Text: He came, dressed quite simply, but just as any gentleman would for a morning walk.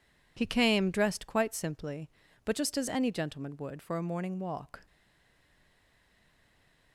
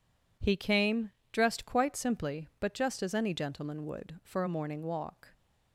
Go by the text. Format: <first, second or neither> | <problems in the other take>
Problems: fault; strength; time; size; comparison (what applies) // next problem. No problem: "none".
second | stays silent after the last word; noticeable; from 4.8 s on; 2.1 s long